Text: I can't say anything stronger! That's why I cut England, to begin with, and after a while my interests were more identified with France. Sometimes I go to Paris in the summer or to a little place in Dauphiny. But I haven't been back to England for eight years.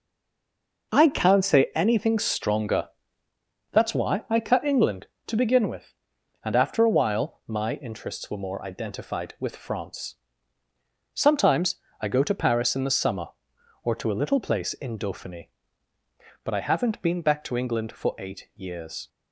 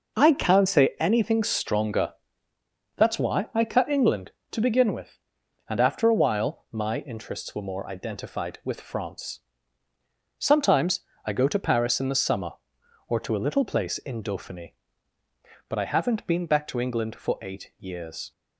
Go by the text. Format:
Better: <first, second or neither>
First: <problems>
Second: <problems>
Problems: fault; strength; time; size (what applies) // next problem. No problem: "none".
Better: second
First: stays silent before the first word; slight; until 0.9 s; 0.9 s long // pauses between "Sometimes" and "I"; slight; at 11.8 s; 0.20 s long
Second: pauses between "Sometimes" and "I"; slight; at 11.0 s; 0.20 s long